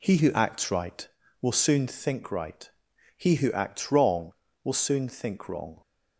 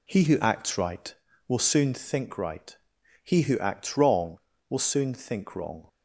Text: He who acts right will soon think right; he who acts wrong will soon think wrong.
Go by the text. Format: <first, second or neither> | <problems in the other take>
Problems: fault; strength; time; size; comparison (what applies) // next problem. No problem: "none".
neither | none